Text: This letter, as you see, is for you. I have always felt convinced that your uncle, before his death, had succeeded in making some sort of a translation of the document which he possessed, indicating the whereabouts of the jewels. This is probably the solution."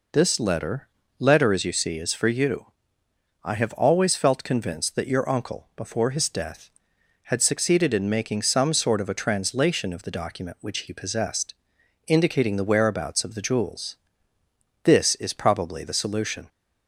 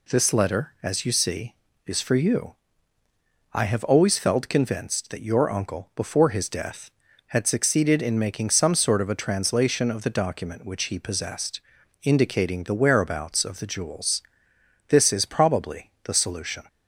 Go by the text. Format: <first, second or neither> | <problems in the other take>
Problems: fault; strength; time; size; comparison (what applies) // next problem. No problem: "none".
second | says "letter" twice; at 1.1 s